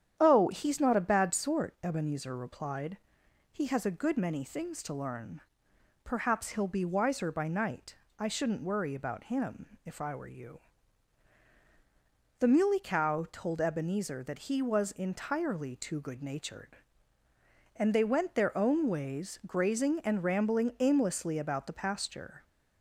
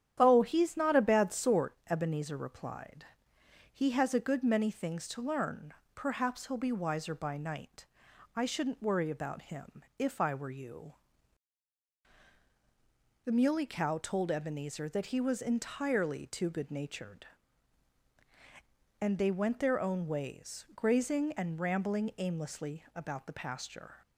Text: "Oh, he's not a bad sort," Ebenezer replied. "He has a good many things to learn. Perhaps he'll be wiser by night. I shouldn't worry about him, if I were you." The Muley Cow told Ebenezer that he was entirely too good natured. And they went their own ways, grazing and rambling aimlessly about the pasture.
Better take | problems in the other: neither | starts louder than the rest; strong; the same in both

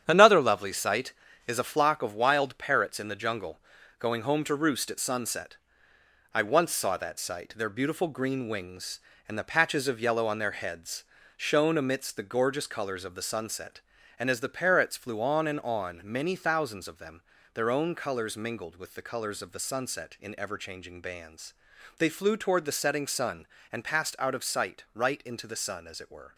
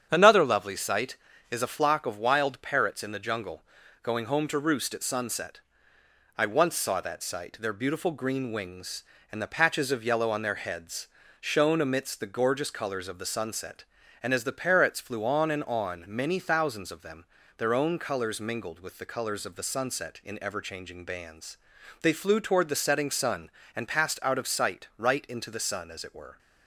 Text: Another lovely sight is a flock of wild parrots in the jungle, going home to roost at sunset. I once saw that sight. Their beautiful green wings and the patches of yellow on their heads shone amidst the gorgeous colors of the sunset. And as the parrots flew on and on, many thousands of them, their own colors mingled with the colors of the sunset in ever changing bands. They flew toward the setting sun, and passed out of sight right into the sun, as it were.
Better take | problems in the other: second | gets quieter; strong; throughout; 7.5 dB // starts louder than the rest; strong; until 1.0 s; 9 dB; strong in the second // pauses between "heads" and "shone"; slight; at 11.0 s; 0.34 s long; slight in the second

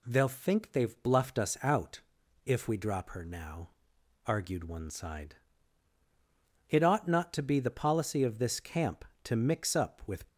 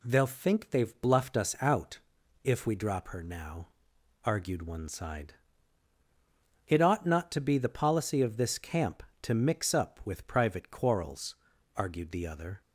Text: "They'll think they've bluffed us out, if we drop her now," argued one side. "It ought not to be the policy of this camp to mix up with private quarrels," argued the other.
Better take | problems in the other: second | stops before "private quarrels argued the other"; at 10.2 s

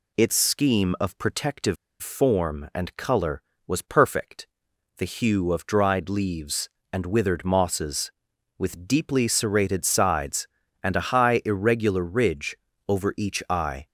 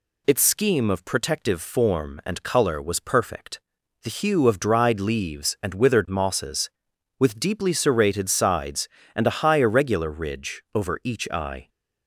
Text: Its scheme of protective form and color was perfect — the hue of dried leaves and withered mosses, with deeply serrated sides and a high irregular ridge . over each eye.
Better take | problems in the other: second | pauses between "protective" and "form"; slight; at 1.7 s; 0.26 s long

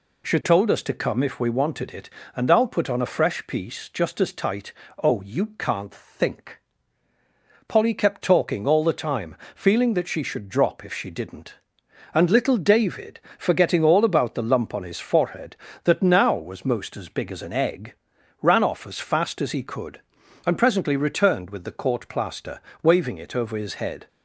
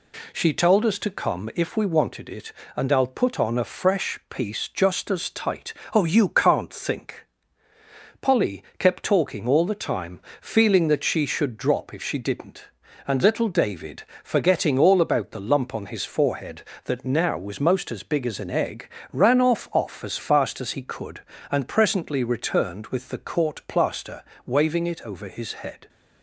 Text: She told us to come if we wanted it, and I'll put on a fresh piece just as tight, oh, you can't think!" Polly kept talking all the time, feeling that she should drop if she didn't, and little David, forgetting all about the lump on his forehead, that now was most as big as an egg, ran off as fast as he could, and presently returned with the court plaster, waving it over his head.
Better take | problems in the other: first | pauses between "Polly" and "kept"; slight; at 8.6 s; 0.16 s long // says "off" twice; at 19.7 s

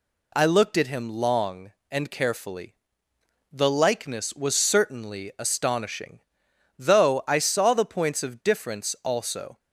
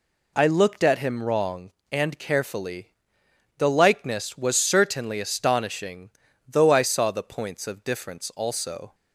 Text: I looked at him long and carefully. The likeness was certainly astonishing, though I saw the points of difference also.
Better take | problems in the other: first | says "wrong" for "long"; at 1.2 s

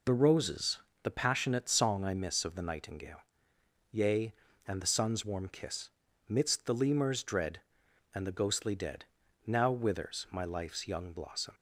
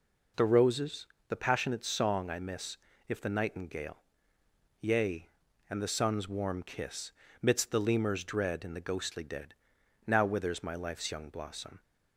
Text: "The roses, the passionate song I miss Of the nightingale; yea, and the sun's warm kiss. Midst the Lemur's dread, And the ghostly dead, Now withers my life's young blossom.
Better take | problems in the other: first | says "If" for "Of"; at 3.0 s

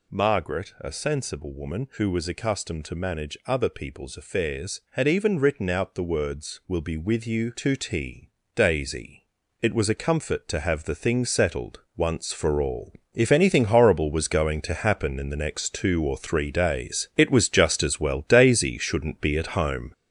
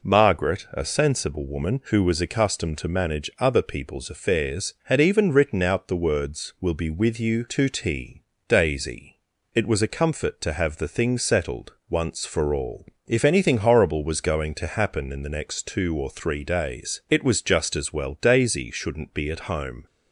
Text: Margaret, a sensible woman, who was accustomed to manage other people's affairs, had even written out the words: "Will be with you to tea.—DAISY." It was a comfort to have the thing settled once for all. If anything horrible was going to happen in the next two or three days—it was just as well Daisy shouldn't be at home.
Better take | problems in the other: second | gets louder; throughout; 6.5 dB

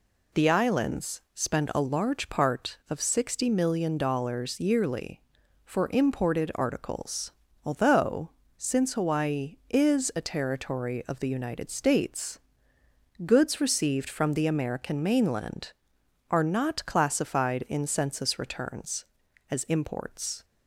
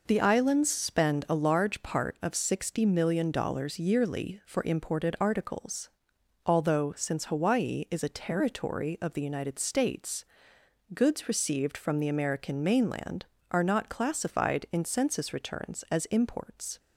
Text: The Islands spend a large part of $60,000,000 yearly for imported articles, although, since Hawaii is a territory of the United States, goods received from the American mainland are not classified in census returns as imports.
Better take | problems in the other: neither | none

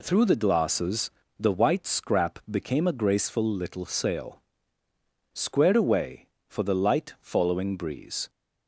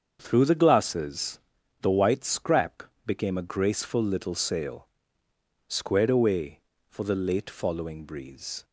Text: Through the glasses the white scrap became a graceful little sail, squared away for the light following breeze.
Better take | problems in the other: first | starts louder than the rest; until 1.2 s; 7 dB // pauses between "glasses" and "the"; at 1.4 s; 0.40 s long; slight in the first // pauses between "scrap" and "became"; slight; at 2.8 s; 0.24 s long // says "late" for "light"; at 7.1 s

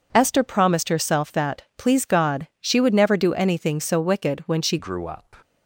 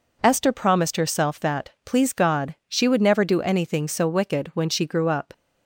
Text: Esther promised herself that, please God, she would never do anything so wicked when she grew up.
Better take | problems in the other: second | changes voice at "grew"; from 4.7 s on; 0.6 s long

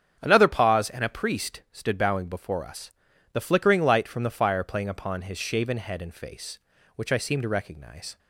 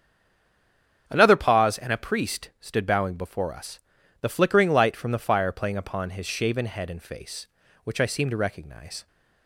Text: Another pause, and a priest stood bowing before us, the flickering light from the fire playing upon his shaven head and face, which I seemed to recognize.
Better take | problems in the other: first | stays silent before the first word; until 1.0 s; 1.0 s long // starts louder than the rest; strong; until 2.0 s; 8.5 dB; strong in the first

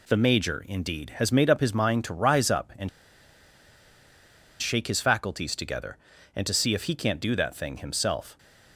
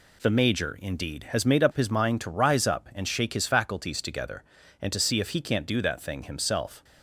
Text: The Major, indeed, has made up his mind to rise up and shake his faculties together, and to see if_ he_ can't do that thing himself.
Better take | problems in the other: second | pauses between "and" and "shake"; strong; at 2.8 s; 1.7 s long

